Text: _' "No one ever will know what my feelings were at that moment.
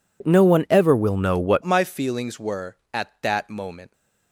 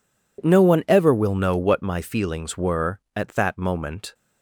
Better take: second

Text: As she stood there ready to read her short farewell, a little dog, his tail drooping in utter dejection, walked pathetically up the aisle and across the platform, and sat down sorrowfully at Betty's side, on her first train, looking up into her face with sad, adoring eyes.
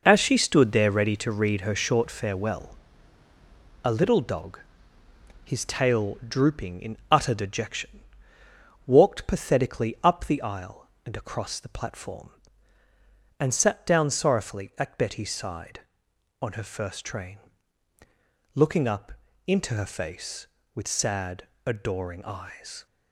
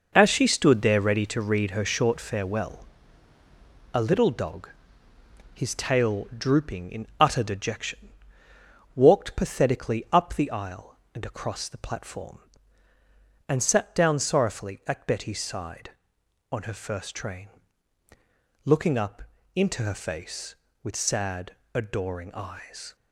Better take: neither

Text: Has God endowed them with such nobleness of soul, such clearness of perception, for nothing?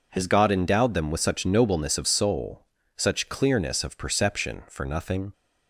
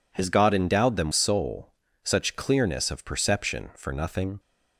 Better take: first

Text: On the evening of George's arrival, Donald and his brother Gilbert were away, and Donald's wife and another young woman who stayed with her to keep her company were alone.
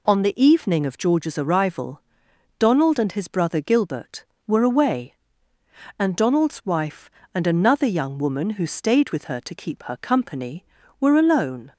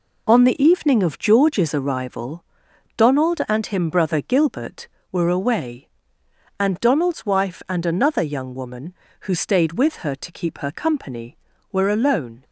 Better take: first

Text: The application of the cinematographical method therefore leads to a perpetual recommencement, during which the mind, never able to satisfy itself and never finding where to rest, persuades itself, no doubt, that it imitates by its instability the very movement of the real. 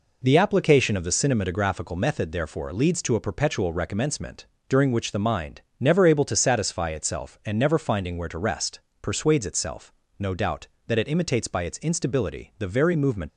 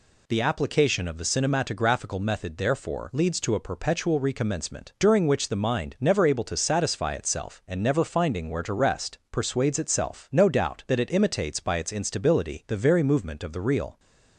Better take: second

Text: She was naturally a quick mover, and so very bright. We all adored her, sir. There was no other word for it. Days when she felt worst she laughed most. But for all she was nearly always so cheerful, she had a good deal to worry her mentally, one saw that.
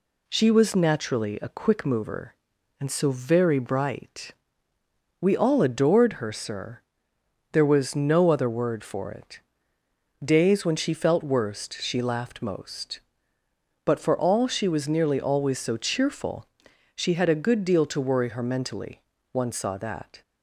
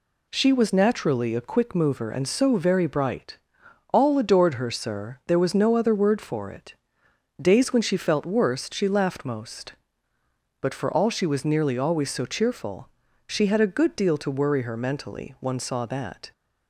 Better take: first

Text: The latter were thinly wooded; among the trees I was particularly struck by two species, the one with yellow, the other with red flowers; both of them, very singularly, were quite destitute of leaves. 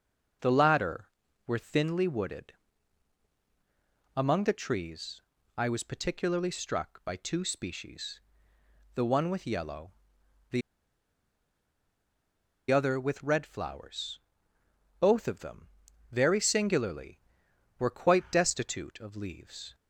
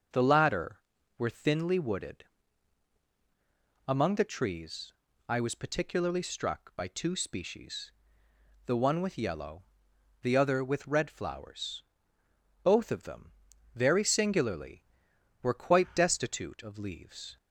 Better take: second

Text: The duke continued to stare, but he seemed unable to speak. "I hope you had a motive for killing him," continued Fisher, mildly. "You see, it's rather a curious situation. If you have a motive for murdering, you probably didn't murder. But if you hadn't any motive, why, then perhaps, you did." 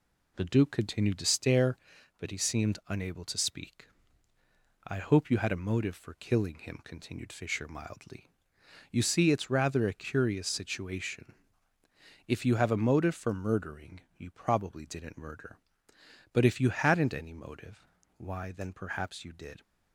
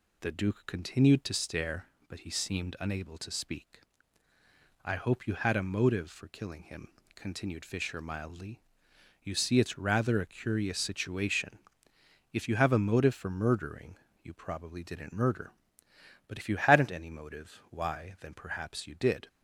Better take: neither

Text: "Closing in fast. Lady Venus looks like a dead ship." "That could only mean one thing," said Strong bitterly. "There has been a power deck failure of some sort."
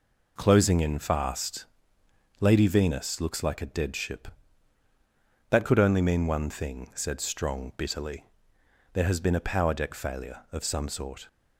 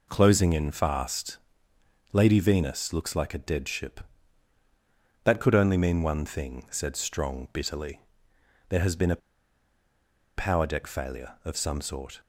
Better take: first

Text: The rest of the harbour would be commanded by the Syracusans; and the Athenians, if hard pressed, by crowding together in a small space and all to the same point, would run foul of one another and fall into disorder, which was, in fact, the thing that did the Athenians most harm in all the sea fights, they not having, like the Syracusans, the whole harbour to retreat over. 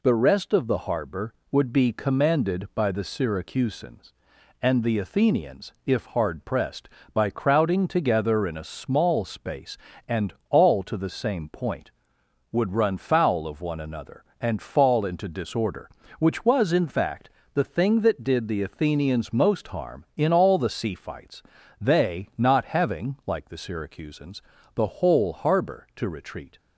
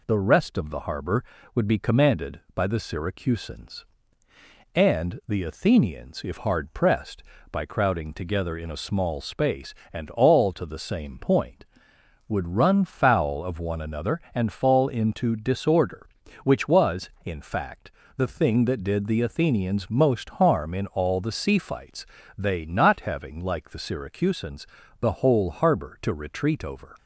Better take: second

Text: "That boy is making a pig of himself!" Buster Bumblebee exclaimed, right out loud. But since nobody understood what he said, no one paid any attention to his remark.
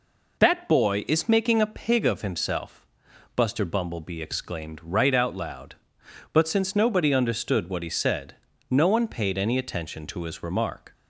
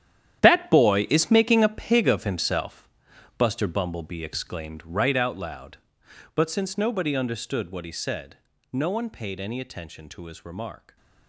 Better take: first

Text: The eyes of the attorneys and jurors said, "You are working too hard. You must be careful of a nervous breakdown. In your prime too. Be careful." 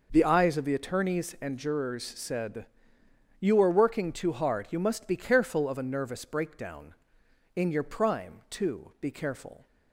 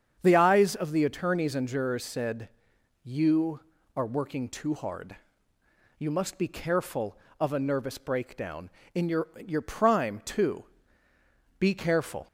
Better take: first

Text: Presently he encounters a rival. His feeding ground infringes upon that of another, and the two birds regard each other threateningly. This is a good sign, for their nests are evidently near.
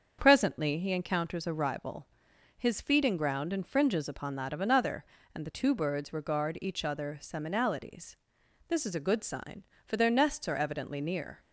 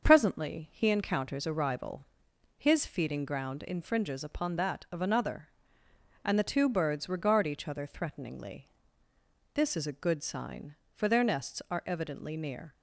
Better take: second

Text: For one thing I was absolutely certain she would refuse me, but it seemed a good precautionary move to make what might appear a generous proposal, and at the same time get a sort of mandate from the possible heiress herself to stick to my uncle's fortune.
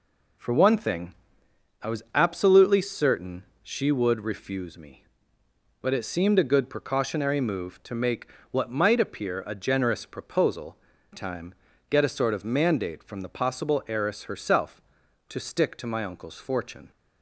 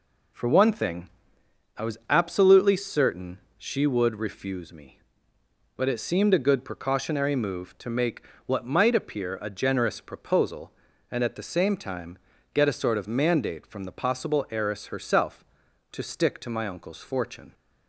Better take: second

